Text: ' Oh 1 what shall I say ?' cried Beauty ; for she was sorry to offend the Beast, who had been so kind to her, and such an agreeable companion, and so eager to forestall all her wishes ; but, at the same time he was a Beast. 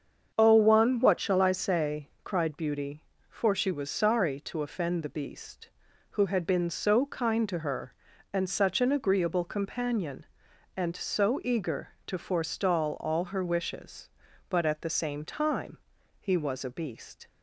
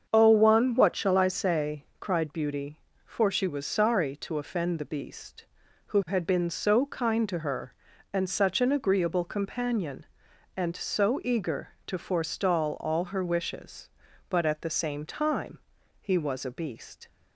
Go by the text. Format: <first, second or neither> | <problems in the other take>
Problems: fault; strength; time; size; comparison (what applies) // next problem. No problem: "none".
neither | starts louder than the rest; the same in both // pauses between "time" and "he"; the same in both